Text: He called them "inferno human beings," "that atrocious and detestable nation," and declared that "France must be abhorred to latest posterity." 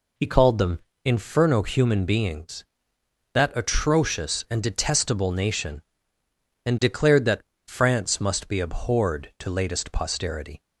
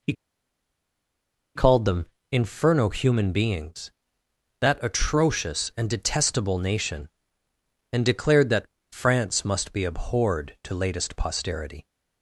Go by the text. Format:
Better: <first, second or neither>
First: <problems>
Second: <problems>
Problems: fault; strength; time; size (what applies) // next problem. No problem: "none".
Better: first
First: pauses between "them" and "inferno"; slight; at 0.7 s; 0.24 s long // pauses between "that" and "France"; slight; at 7.4 s; 0.26 s long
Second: pauses between "He" and "called"; strong; at 0.1 s; 1.4 s long // pauses between "them" and "inferno"; slight; at 2.0 s; 0.24 s long // pauses between "that" and "France"; slight; at 8.6 s; 0.26 s long